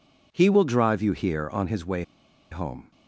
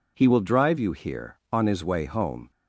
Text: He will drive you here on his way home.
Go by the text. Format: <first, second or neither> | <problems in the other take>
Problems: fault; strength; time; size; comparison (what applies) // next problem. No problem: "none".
second | pauses between "way" and "home"; noticeable; at 2.0 s; 0.47 s long